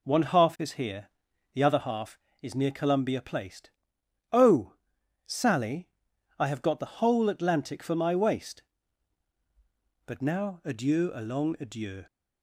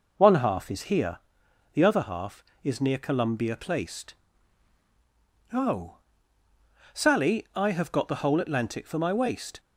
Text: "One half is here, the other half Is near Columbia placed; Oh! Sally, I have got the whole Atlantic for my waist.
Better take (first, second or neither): second